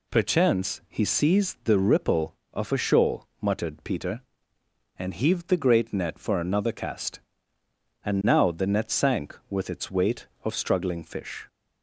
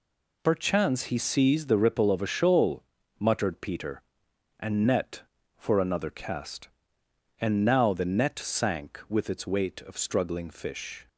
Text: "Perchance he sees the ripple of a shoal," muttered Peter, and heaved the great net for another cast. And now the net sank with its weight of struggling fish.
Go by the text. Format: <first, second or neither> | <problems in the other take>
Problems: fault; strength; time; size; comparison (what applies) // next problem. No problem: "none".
first | skips "heaved the great"; at 4.8 s